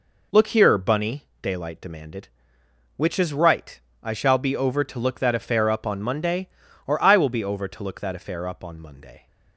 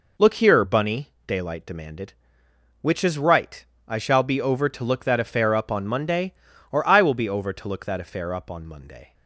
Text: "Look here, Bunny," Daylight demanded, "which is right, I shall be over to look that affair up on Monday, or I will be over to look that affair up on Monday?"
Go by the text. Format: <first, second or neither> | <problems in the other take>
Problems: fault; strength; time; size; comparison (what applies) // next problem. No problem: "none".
neither | none